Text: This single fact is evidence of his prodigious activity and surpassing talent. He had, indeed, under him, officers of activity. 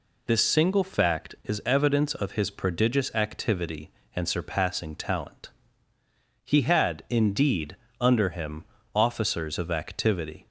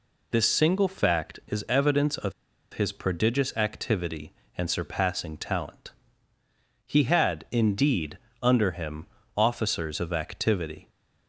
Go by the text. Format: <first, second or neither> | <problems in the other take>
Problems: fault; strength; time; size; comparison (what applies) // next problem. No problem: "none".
first | pauses between "of" and "his"; at 2.3 s; 0.41 s long